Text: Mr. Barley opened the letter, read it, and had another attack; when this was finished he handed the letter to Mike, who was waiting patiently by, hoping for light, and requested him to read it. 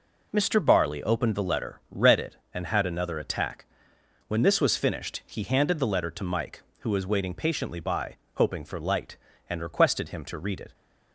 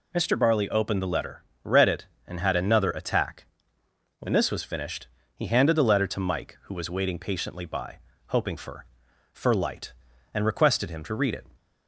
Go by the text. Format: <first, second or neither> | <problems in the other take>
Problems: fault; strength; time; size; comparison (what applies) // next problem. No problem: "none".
first | pauses between "finished" and "he"; slight; at 5.0 s; 0.28 s long // says "for" twice; at 9.3 s